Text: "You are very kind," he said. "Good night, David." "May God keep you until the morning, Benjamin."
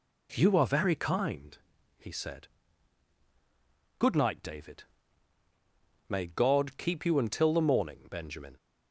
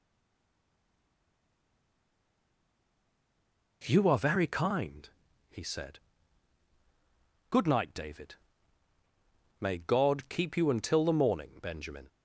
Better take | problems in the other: first | stays silent before the first word; strong; until 3.8 s; 3.8 s long

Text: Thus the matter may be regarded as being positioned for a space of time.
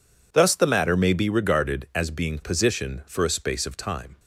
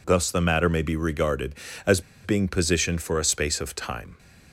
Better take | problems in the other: first | pauses between "as" and "being"; slight; at 1.9 s; 0.24 s long

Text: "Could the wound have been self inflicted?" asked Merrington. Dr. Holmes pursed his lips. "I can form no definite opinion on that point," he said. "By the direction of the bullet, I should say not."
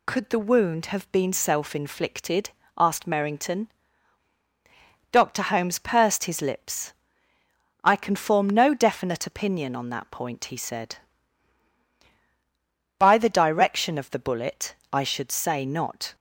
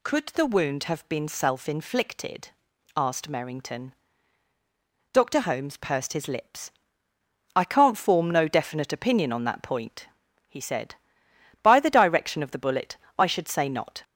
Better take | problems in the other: first | says "can't" for "can"; at 7.6 s

